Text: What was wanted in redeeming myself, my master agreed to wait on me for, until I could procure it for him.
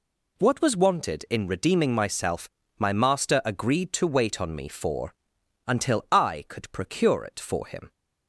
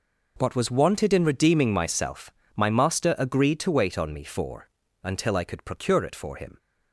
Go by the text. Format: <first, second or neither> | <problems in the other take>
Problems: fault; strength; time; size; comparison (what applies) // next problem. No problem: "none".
neither | none